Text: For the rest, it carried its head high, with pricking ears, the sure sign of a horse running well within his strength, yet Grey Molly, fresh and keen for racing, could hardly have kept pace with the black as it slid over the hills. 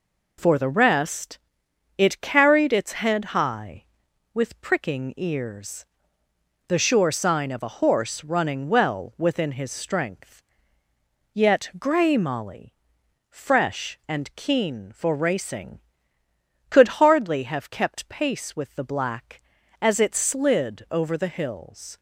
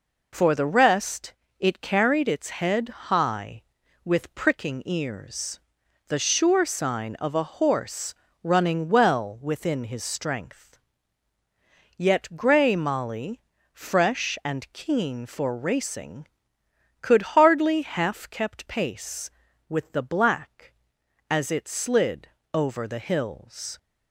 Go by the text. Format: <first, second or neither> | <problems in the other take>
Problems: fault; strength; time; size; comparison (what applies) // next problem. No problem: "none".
first | pauses between "horse" and "running"; slight; at 8.1 s; 0.26 s long // says "half" for "have"; at 17.8 s // pauses between "slid" and "over"; slight; at 22.2 s; 0.26 s long